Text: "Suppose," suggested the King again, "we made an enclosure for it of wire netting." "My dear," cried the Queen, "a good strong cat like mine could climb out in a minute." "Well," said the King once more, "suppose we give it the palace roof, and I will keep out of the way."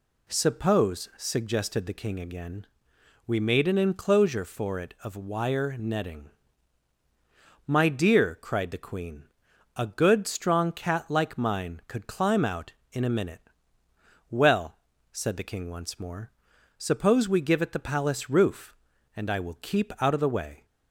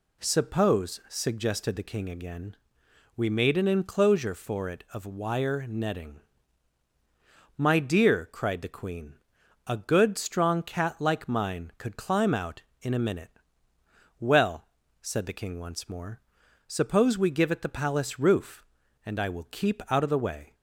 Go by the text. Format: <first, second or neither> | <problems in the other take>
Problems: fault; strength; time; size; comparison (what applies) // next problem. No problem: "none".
neither | none